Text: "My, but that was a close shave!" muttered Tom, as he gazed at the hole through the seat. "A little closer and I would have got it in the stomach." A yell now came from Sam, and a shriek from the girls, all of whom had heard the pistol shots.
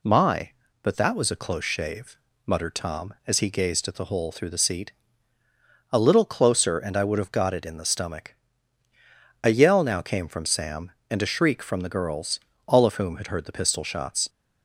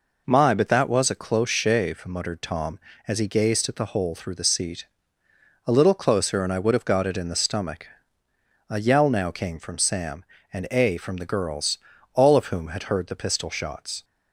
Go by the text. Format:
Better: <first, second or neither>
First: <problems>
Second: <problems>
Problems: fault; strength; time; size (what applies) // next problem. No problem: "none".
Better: first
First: none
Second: skips "shriek"; at 10.9 s